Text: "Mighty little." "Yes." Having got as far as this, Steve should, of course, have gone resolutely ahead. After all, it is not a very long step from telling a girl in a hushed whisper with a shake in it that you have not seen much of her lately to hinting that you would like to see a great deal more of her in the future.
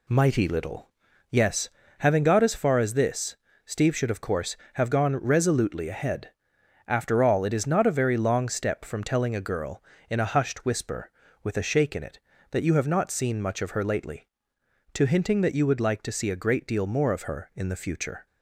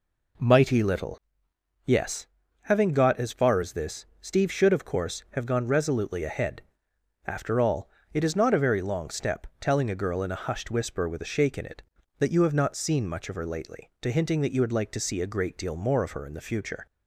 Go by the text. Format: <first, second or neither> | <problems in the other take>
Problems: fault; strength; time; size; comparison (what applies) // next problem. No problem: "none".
first | skips "from"; at 9.5 s